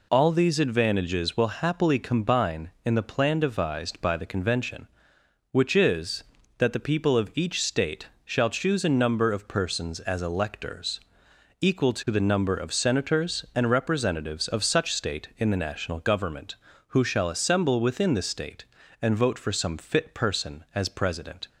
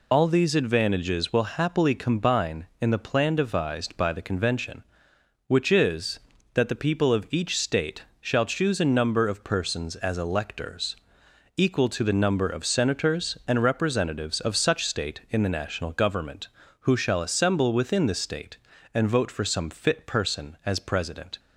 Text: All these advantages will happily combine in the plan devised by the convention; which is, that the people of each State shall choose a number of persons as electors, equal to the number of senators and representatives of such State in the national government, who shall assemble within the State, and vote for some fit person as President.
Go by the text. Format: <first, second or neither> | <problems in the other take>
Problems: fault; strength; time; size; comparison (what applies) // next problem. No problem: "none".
first | loses the start of "All"; at 0.1 s; 50 ms // pauses between "State" and "shall"; slight; at 8.0 s; 0.18 s long; slight in the first